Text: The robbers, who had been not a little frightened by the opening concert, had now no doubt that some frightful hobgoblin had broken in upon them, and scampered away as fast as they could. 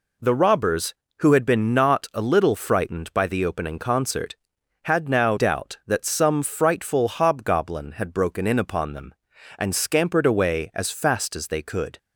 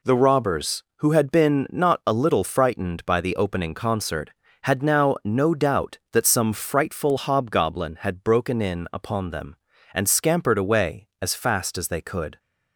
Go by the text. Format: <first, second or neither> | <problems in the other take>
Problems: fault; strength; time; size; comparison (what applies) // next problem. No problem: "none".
second | skips "no"; at 5.3 s